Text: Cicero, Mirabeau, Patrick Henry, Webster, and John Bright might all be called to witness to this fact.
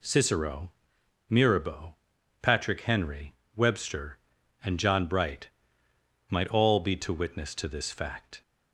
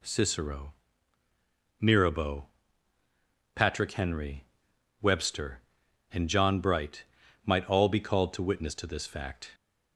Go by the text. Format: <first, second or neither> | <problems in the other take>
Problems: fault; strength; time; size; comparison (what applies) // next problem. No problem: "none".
second | pauses between "Bright" and "might"; noticeable; at 5.4 s; 0.78 s long; also in the second // skips "called"; at 6.9 s